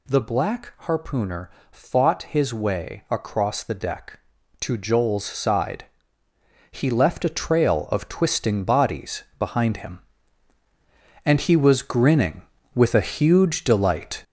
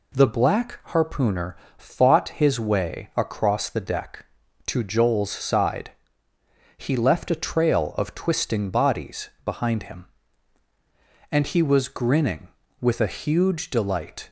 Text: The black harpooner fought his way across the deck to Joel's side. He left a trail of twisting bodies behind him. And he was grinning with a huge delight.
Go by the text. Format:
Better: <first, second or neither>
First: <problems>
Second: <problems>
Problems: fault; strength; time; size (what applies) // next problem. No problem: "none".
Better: second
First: gets louder; noticeable; throughout; 6 dB // pauses between "harpooner" and "fought"; slight; at 1.4 s; 0.22 s long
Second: pauses between "harpooner" and "fought"; slight; at 1.5 s; 0.22 s long